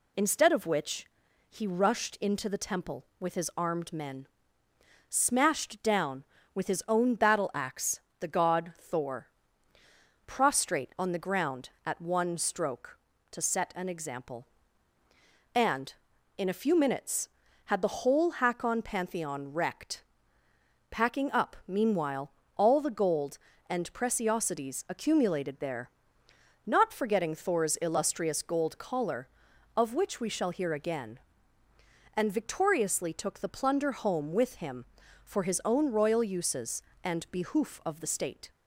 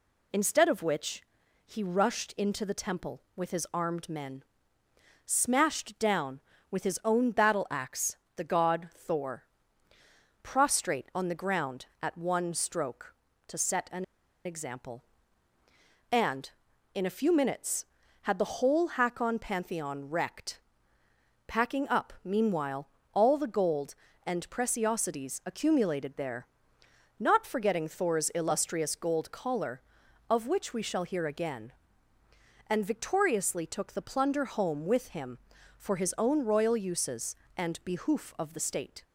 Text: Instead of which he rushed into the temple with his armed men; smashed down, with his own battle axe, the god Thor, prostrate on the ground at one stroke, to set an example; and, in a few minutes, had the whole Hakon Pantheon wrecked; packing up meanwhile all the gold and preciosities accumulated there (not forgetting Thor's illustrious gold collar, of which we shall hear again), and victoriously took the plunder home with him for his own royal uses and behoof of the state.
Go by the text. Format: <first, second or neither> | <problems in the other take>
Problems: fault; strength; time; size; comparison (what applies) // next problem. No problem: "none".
first | pauses between "which" and "he"; at 1.2 s; 0.42 s long; also in the first // pauses between "an" and "example"; at 14.0 s; 0.40 s long // pauses between "meanwhile" and "all"; slight; at 22.8 s; 0.26 s long; slight in the first